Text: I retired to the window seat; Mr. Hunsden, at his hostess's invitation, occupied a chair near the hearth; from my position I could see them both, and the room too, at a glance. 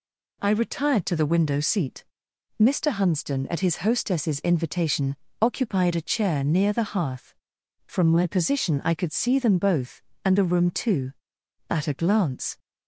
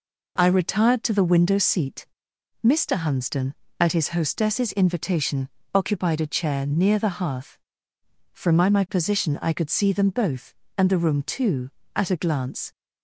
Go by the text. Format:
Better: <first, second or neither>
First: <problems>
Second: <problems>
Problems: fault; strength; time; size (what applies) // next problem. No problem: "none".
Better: first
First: none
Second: says "my" twice; at 8.6 s